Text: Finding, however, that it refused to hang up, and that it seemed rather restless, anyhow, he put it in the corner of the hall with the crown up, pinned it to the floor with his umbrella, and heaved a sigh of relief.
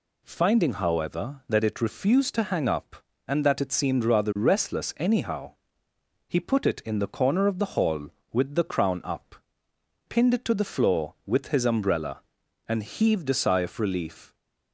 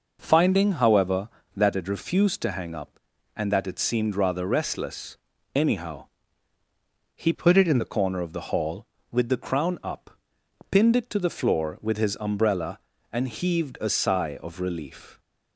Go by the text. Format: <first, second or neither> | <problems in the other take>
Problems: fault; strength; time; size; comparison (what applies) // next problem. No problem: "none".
first | changes voice from "put" to "in"; from 7.3 to 7.7 s; 0.4 s long